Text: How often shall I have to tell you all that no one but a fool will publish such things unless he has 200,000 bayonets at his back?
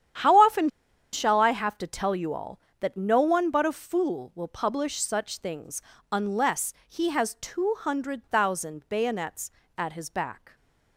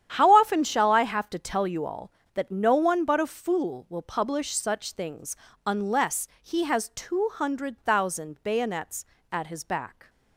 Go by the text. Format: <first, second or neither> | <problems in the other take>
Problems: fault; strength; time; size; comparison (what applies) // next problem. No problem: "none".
second | starts louder than the rest; strong; until 1.6 s; 10 dB; strong in the second // pauses between "often" and "shall"; at 0.6 s; 0.43 s long // pauses between "things" and "unless"; slight; at 5.8 s; 0.30 s long; slight in the second // pauses between "unless" and "he"; slight; at 6.7 s; 0.16 s long; slight in the second